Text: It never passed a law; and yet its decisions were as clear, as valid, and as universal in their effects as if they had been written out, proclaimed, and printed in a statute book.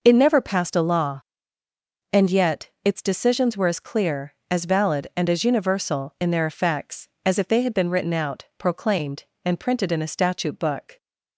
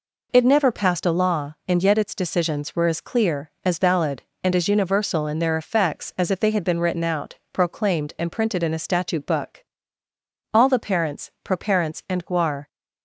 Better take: first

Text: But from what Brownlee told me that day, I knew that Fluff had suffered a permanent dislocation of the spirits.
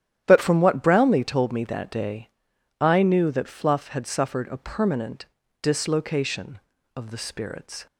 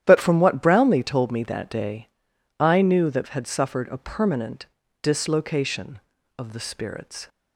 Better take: first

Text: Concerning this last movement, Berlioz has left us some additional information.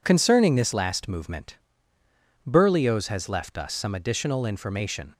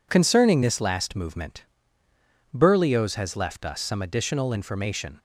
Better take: neither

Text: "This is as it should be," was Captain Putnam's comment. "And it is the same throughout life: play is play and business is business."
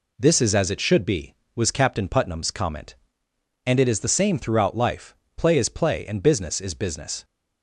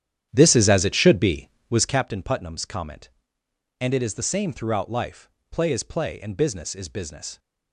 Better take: first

